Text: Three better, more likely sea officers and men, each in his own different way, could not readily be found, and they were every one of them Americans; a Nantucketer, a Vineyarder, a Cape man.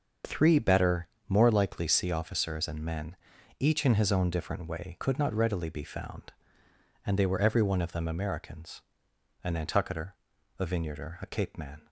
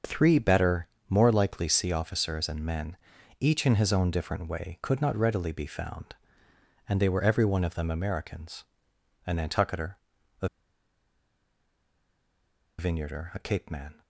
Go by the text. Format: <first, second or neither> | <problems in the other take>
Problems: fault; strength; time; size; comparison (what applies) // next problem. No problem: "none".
first | starts louder than the rest; until 1.2 s; 6.5 dB; also in the first // pauses between "a" and "Vineyarder"; strong; at 10.4 s; 2.3 s long